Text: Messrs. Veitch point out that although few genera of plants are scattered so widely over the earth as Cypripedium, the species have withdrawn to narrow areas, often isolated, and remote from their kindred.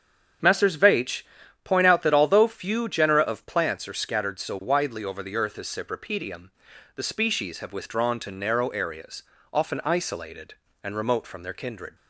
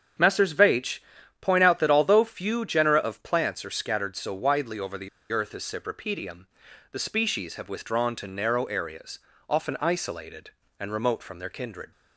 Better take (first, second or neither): first